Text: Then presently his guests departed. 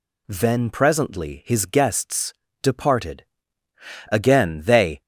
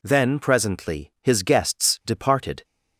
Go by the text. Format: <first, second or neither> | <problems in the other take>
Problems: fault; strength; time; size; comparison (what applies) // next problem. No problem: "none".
second | pauses between "guests" and "departed"; slight; at 2.3 s; 0.28 s long // goes on to say "Again they"; noticeable; from 4.1 s on; 0.90 s long